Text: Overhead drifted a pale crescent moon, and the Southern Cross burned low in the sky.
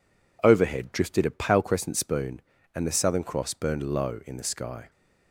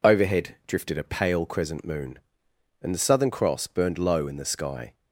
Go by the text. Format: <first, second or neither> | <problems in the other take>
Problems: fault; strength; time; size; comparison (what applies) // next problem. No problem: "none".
second | says "spoon" for "moon"; at 1.9 s